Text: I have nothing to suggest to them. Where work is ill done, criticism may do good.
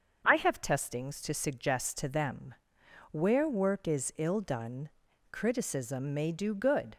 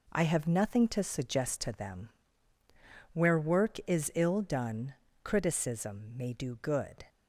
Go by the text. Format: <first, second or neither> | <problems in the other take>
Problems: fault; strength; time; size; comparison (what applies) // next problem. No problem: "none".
second | starts louder than the rest; until 1.2 s; 6.5 dB // says "testings" for "nothing"; at 0.6 s